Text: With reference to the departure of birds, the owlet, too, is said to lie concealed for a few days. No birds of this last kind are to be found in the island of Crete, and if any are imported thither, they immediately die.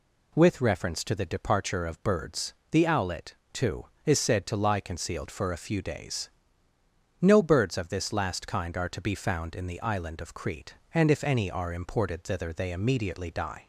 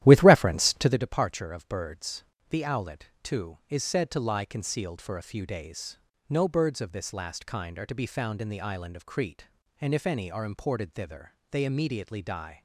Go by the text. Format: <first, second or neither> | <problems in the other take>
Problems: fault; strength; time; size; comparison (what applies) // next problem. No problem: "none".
first | starts louder than the rest; strong; until 1.0 s; 13 dB